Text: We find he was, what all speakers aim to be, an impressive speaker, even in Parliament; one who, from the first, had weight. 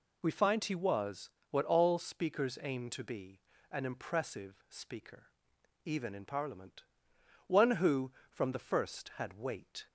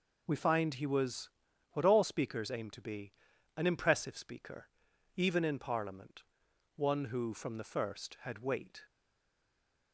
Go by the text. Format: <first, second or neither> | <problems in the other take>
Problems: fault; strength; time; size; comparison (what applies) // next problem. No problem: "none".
first | stays silent after the last word; from 8.8 s on; 1.1 s long